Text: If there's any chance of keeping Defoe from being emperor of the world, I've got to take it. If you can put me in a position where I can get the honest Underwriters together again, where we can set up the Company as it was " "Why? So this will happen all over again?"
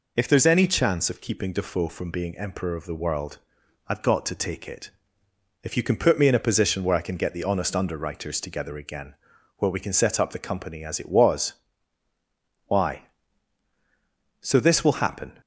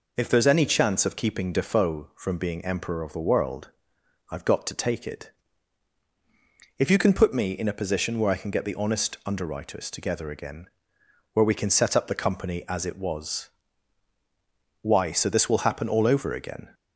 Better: second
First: stops before "all over again"; at 15.4 s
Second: none

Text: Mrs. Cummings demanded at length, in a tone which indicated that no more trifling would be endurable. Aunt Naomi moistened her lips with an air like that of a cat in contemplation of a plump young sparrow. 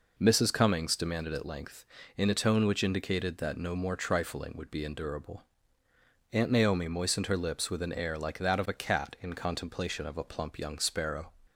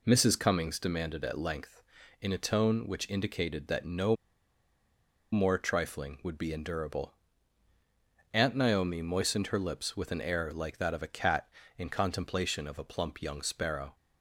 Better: first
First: none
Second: pauses between "no" and "more"; at 4.1 s; 1.1 s long

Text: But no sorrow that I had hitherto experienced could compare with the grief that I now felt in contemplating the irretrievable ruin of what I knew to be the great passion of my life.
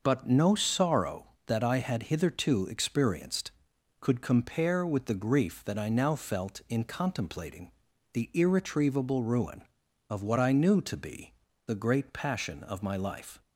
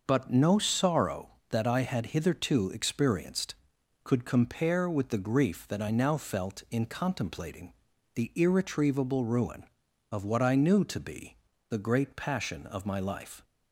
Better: neither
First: starts louder than the rest; noticeable; until 1.0 s; 6 dB // pauses between "contemplating" and "the"; at 7.7 s; 0.42 s long // pauses between "be" and "the"; slight; at 11.3 s; 0.34 s long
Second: starts louder than the rest; noticeable; until 1.0 s; 6 dB // pauses between "contemplating" and "the"; at 7.7 s; 0.42 s long // pauses between "be" and "the"; slight; at 11.3 s; 0.34 s long

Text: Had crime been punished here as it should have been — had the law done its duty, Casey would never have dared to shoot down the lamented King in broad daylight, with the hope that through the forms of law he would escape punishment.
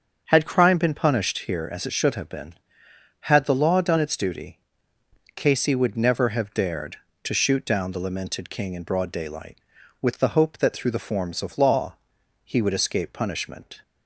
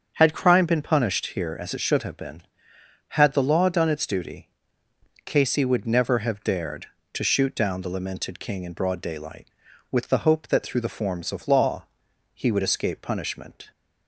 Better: neither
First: starts louder than the rest; until 1.2 s; 7 dB // pauses between "law" and "he"; noticeable; at 11.9 s; 0.48 s long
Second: starts louder than the rest; until 1.1 s; 7 dB // pauses between "law" and "he"; noticeable; at 11.8 s; 0.48 s long

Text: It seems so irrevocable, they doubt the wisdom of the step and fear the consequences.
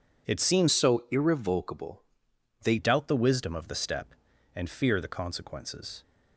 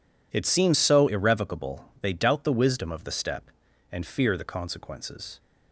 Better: second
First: changes voice from "so" to "they"; from 0.7 to 2.7 s; 2.0 s long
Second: none

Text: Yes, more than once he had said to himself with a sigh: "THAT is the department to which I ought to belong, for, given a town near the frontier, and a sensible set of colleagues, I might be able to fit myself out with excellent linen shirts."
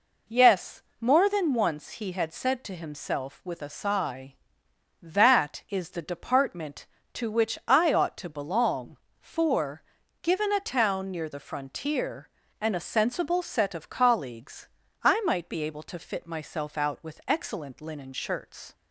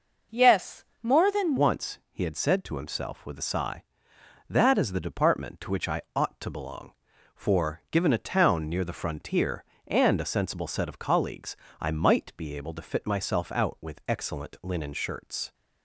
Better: first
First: none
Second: changes voice at "once"; from 1.5 s on; 14.0 s long

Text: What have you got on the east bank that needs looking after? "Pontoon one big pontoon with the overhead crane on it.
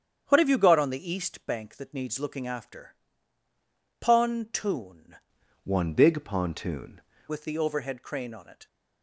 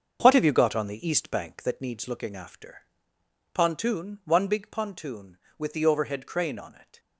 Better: second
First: starts louder than the rest; strong; until 1.2 s; 8.5 dB // changes voice from "one" to "pontoon"; from 5.6 to 7.0 s; 1.4 s long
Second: starts louder than the rest; until 1.2 s; 7 dB

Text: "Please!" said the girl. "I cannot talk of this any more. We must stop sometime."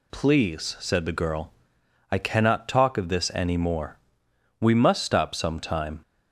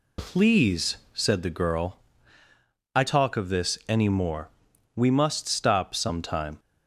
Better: first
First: none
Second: skips "cannot"; at 3.0 s

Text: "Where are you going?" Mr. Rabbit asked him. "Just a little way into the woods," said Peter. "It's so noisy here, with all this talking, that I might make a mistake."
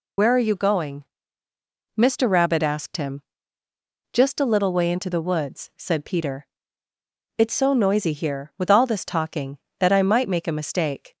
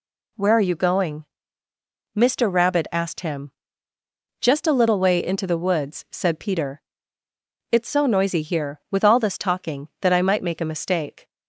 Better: second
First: loses the start of "Where"; at 0.1 s; 70 ms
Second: none

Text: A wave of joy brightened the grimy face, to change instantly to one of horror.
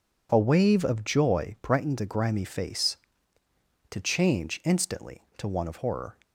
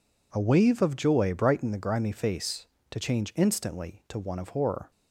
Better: neither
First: none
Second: none

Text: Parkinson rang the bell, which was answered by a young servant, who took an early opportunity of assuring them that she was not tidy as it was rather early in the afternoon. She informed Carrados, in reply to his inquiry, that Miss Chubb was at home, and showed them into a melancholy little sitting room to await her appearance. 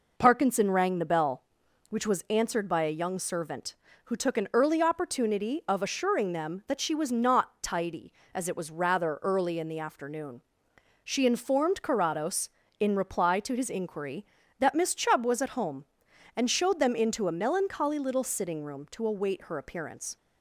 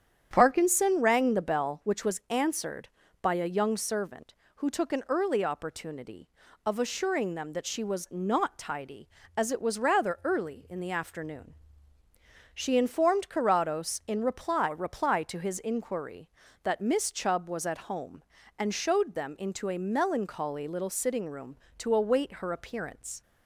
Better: first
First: none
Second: starts louder than the rest; strong; until 1.3 s; 9 dB // says "reply" twice; at 14.6 s

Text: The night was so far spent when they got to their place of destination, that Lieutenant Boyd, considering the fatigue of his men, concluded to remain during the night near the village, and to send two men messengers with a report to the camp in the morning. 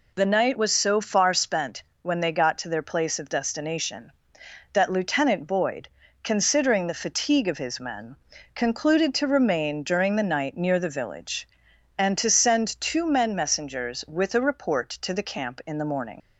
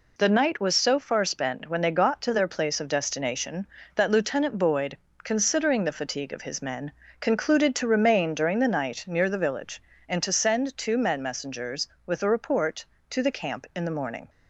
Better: second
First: pauses between "spent" and "when"; slight; at 1.8 s; 0.18 s long // leaves "morning" unfinished; at 16.1 s; 110 ms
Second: none

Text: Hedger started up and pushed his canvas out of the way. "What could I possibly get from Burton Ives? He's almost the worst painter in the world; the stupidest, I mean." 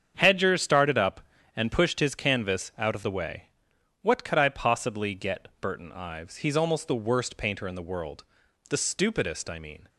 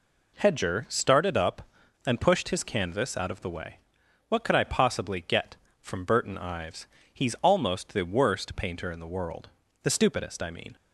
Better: second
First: starts louder than the rest; strong; until 1.1 s; 8 dB // skips "from"; at 5.5 s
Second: none

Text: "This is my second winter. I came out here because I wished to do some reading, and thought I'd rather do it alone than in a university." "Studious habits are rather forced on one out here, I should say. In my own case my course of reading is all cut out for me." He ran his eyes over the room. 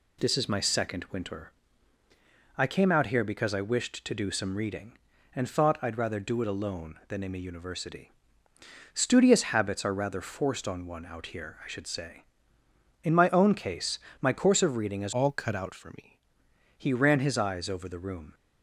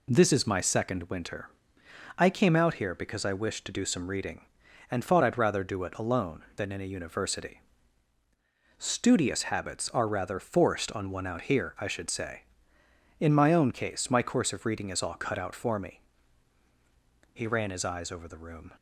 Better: second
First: pauses between "case" and "my"; slight; at 13.9 s; 0.22 s long // changes voice from "all" to "me"; from 15.1 to 16.1 s; 1.0 s long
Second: none

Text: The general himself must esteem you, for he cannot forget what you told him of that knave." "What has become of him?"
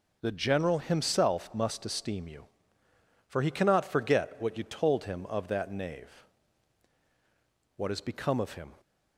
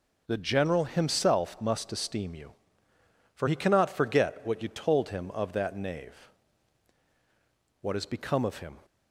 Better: neither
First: none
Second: none

